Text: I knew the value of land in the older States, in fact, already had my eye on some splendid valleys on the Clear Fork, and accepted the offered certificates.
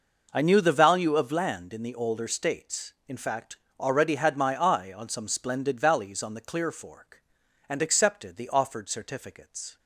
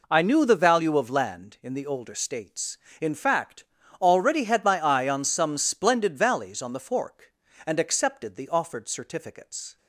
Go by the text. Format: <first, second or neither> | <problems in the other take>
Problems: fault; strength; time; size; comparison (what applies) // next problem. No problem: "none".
first | skips "Clear"; at 6.7 s